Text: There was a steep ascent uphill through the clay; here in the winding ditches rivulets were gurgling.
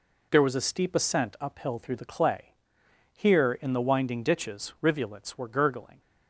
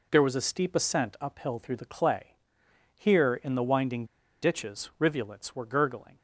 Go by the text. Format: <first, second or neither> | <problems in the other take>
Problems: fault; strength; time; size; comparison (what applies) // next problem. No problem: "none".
first | pauses between "winding" and "ditches"; at 4.0 s; 0.37 s long